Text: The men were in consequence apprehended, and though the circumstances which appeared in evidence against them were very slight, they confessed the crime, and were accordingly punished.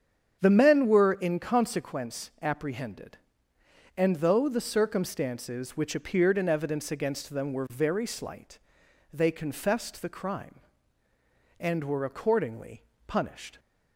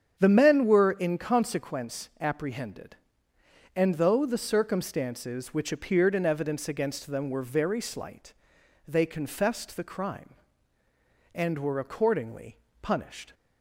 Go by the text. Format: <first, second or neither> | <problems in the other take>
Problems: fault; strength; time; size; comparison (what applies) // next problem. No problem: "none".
neither | starts louder than the rest; strong; the same in both // pauses between "accordingly" and "punished"; slight; the same in both